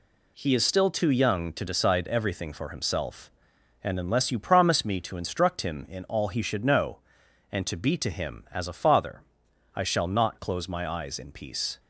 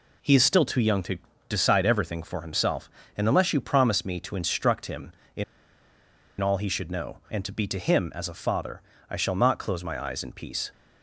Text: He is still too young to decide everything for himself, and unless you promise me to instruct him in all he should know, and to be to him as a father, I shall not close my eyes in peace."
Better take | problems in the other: first | pauses between "to" and "decide"; slight; at 1.1 s; 0.32 s long // pauses between "in" and "all"; at 5.4 s; 0.99 s long

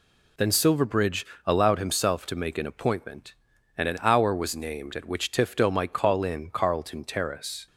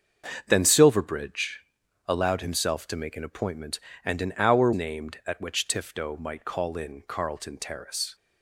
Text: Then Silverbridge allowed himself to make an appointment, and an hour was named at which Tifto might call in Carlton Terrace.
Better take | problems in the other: first | starts louder than the rest; until 1.4 s; 6.5 dB // pauses between "Silverbridge" and "allowed"; noticeable; at 1.6 s; 0.46 s long; slight in the first // skips "was"; at 4.7 s

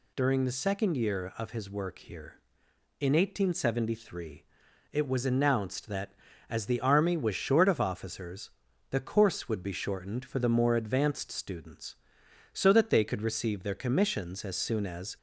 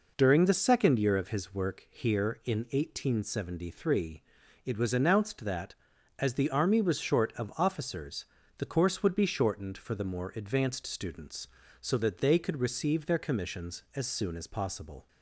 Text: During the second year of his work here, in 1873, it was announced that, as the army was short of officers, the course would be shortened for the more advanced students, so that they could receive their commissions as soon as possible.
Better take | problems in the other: second | stops before "possible"; at 15.1 s

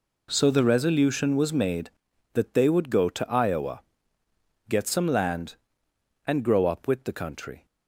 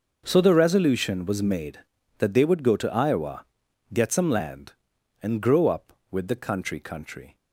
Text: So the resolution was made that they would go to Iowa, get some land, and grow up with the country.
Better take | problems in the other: first | says "country" twice; at 6.8 s

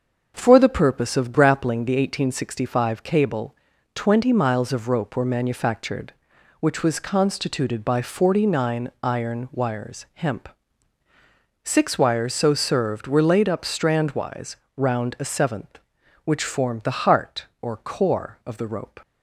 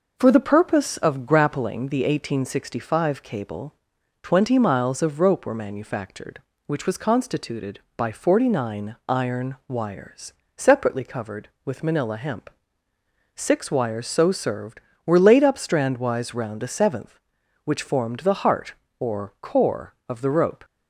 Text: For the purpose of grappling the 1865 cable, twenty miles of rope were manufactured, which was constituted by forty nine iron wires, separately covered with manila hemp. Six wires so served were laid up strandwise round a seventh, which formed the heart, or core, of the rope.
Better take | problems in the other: second | starts louder than the rest; until 1.3 s; 6.5 dB // skips "separately covered with manila"; at 10.0 s // pauses between "strandwise" and "round"; slight; at 14.5 s; 0.20 s long

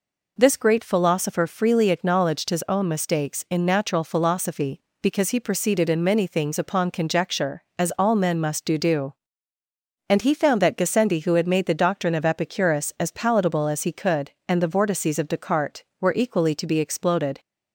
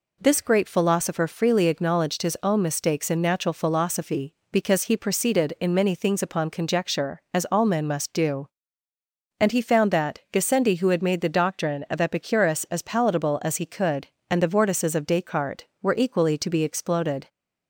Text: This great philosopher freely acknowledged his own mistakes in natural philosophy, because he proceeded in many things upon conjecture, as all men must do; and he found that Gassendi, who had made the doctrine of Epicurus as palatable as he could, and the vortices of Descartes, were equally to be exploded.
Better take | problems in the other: second | says "do" twice; at 8.7 s

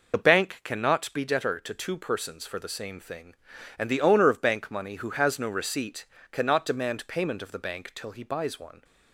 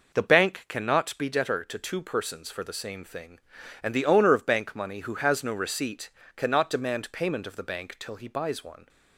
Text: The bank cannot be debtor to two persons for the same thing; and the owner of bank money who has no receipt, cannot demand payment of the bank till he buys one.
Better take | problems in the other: second | loses the start of "The"; at 0.1 s; 40 ms

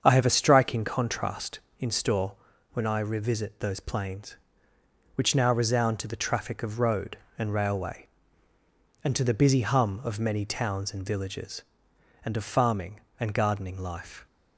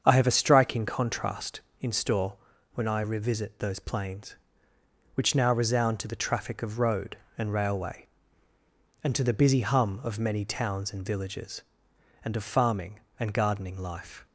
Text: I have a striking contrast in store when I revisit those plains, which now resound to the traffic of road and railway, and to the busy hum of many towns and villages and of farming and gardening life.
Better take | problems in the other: neither | starts louder than the rest; strong; the same in both // pauses between "store" and "when"; the same in both

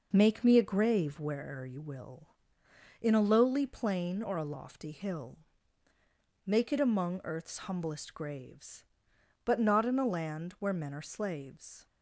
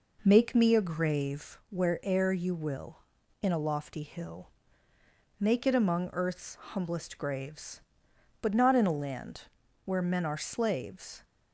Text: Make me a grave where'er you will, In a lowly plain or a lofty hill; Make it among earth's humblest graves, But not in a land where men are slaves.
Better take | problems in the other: first | skips "a lowly plain or"; at 3.5 s // pauses between "land" and "where"; at 9.4 s; 0.42 s long

